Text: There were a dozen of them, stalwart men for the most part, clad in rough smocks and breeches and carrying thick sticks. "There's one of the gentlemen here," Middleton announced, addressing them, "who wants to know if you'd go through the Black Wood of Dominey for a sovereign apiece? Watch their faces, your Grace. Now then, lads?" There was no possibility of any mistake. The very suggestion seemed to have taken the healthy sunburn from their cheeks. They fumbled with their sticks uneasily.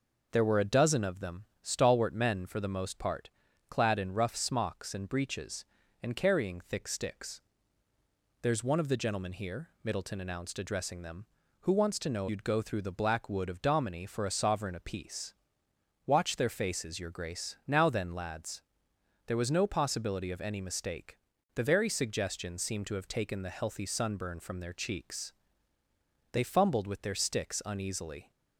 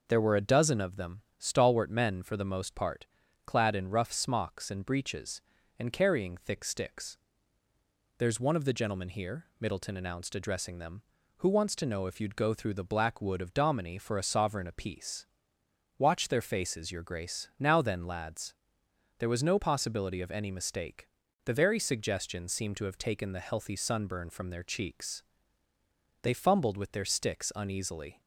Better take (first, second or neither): second